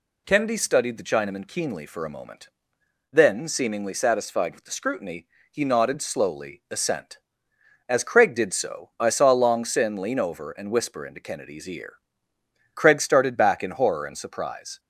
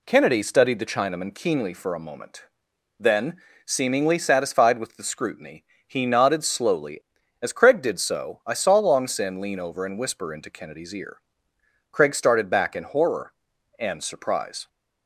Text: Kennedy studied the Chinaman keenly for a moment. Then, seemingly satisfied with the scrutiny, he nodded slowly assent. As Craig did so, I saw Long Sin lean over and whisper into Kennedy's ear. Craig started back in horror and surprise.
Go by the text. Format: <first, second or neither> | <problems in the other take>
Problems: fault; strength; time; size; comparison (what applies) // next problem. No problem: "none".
first | skips "assent"; at 7.2 s